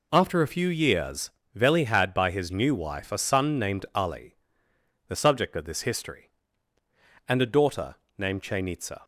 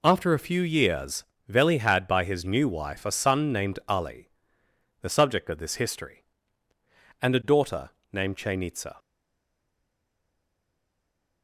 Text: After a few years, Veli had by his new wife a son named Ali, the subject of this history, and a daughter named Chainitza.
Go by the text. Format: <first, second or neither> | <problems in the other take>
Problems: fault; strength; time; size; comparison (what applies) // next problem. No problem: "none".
first | pauses between "daughter" and "named"; slight; at 7.8 s; 0.24 s long; slight in the first // stays silent after the last word; from 8.9 s on; 2.5 s long